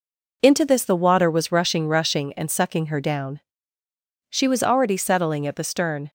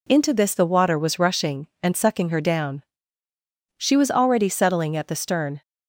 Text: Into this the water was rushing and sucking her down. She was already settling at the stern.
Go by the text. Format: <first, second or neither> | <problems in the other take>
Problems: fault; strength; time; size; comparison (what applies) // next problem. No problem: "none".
second | says "rushing" twice; at 1.8 s